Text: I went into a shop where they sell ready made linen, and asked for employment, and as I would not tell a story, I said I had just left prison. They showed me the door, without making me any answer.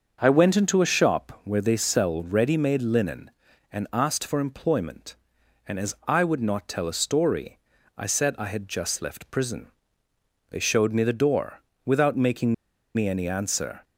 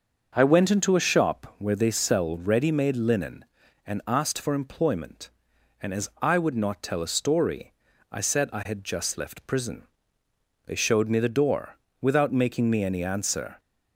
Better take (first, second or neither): second